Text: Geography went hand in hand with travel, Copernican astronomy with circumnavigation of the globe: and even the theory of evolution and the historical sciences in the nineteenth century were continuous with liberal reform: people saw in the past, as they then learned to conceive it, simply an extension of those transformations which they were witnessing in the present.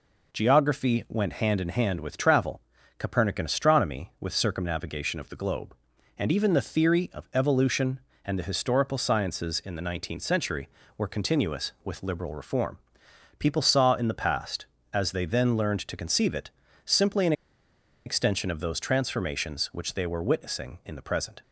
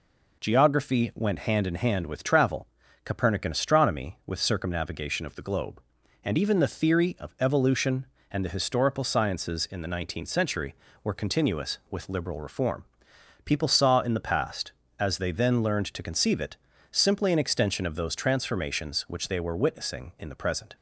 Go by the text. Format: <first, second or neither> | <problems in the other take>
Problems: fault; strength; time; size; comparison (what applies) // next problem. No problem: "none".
second | pauses between "an" and "extension"; noticeable; at 17.3 s; 0.73 s long